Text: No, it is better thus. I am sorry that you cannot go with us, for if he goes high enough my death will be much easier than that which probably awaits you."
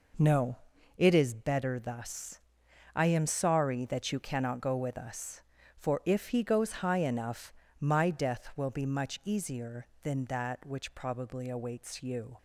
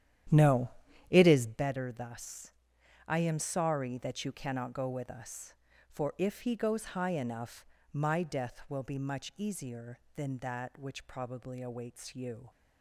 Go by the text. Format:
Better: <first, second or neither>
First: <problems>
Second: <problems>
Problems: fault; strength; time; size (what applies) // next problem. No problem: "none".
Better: first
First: pauses between "enough" and "my"; slight; at 7.5 s; 0.30 s long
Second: starts louder than the rest; strong; until 1.7 s; 10.5 dB // pauses between "enough" and "my"; slight; at 7.6 s; 0.30 s long